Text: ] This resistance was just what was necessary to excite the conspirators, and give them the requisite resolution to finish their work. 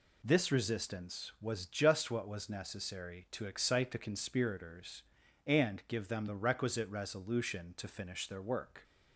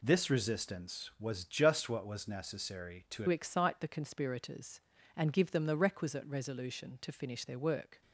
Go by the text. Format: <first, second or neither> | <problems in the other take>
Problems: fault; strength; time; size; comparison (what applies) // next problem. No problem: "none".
first | changes voice at "excite"; from 3.2 s on; 4.8 s long